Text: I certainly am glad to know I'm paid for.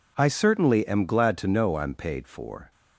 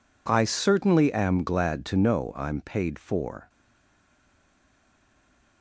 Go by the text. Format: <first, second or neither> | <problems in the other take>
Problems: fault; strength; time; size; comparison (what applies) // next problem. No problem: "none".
first | stays silent after the last word; from 3.4 s on; 2.2 s long